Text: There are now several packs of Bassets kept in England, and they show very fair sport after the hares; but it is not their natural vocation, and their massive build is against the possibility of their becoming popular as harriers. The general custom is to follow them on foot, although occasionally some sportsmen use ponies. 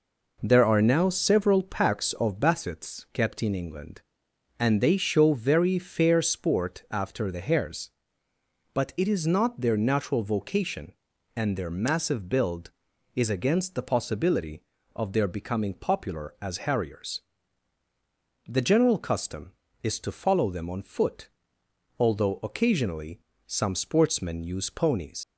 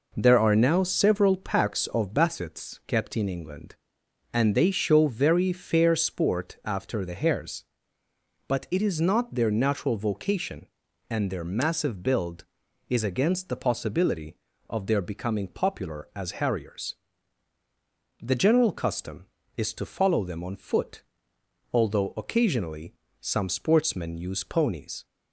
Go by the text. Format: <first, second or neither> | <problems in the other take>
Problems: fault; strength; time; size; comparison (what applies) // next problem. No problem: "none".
second | pauses between "occasionally" and "some"; slight; at 23.1 s; 0.26 s long; slight in the second // leaves "ponies" unfinished; at 25.2 s; 75 ms